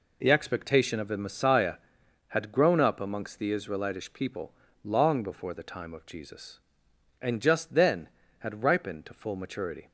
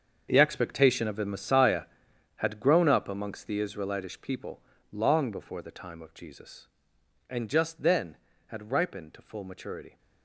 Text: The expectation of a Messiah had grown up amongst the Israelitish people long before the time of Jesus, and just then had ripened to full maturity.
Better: first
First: pauses between "people" and "long"; slight; at 4.5 s; 0.30 s long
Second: gets quieter; strong; throughout; 14.5 dB // pauses between "people" and "long"; slight; at 4.6 s; 0.30 s long

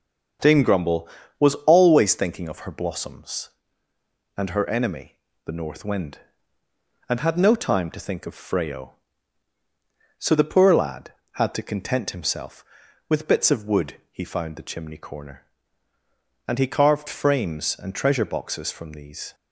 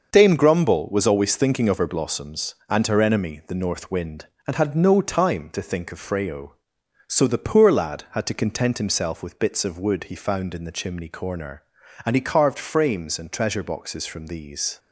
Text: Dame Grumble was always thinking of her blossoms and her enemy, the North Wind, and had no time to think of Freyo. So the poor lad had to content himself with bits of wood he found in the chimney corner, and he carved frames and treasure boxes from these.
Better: second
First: starts louder than the rest; until 1.8 s; 7 dB // skips "in"; at 14.5 s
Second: starts louder than the rest; until 1.1 s; 6 dB

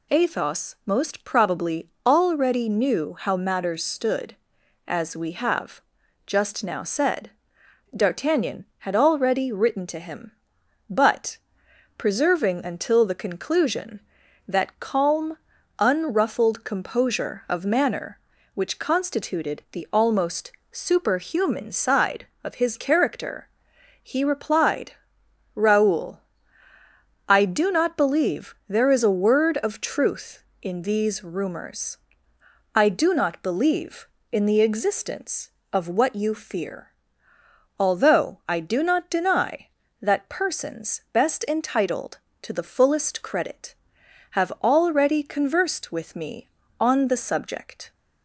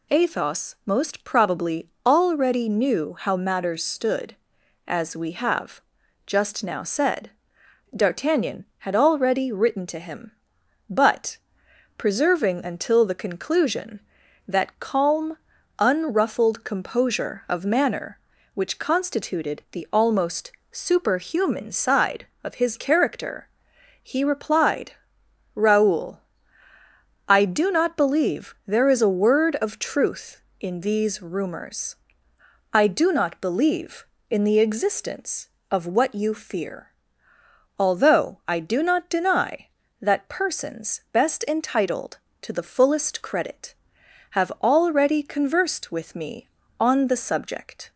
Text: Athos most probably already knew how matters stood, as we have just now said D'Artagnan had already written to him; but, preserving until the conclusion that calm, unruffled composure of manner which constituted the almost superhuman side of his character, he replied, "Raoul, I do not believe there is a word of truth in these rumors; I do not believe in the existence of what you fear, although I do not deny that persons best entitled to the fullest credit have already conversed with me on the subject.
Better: neither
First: pauses between "probably" and "already"; slight; at 1.8 s; 0.16 s long // pauses between "have" and "just"; noticeable; at 5.8 s; 0.46 s long // pauses between "said" and "D'Artagnan"; noticeable; at 7.3 s; 0.64 s long // pauses between "almost" and "superhuman"; slight; at 20.5 s; 0.18 s long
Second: pauses between "probably" and "already"; slight; at 1.8 s; 0.16 s long // pauses between "have" and "just"; noticeable; at 5.8 s; 0.46 s long // pauses between "said" and "D'Artagnan"; noticeable; at 7.3 s; 0.64 s long // pauses between "almost" and "superhuman"; slight; at 20.5 s; 0.18 s long

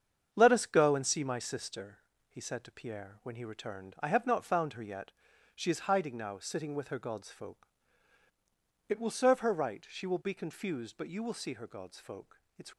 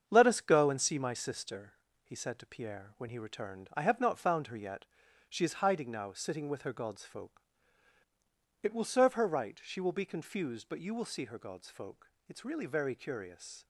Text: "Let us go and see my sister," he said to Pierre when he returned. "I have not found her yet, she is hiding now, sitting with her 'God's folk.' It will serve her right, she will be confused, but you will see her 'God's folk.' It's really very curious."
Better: second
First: starts louder than the rest; strong; until 1.3 s; 7.5 dB // stops before "really very curious"; at 12.7 s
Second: starts louder than the rest; strong; until 1.0 s; 7.5 dB

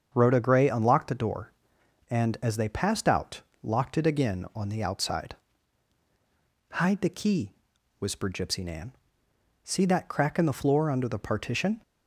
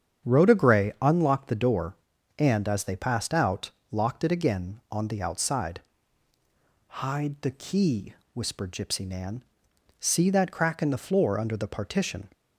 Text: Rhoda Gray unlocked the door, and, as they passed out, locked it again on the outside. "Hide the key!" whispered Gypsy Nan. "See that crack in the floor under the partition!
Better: neither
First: starts louder than the rest; until 1.1 s; 7 dB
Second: starts louder than the rest; strong; until 1.3 s; 8 dB

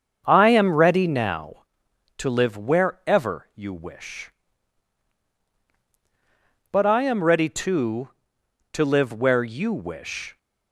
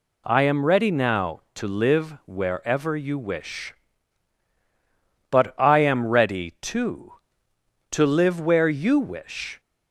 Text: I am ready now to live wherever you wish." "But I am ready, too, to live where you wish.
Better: second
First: starts louder than the rest; until 1.4 s; 7 dB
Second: none

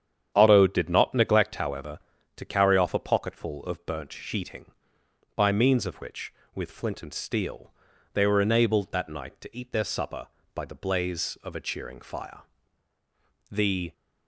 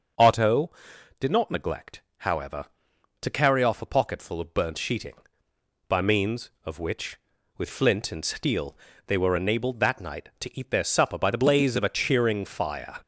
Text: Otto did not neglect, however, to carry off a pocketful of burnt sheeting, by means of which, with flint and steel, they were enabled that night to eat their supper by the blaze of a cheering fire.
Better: second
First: starts louder than the rest; strong; until 1.3 s; 8.5 dB // goes on to say "The"; slight; from 13.5 s on; 0.42 s long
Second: none

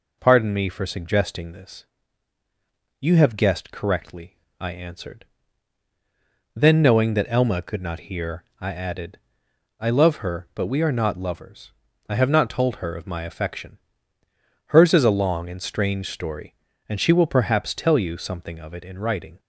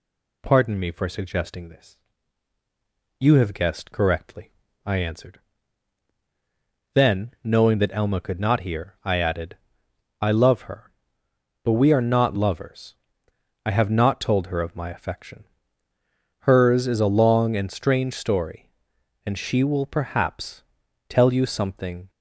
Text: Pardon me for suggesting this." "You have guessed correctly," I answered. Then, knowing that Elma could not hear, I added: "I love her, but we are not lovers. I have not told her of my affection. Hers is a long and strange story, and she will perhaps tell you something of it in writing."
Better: first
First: none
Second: pauses between "perhaps" and "tell"; noticeable; at 20.6 s; 0.46 s long // stops before "of it in writing"; at 22.0 s

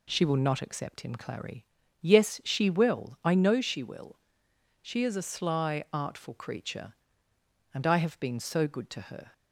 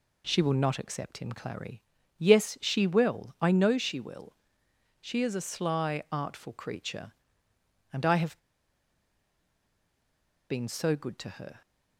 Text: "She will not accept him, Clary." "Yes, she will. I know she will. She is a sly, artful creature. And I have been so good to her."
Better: first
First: none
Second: pauses between "have" and "been"; strong; at 8.3 s; 2.1 s long

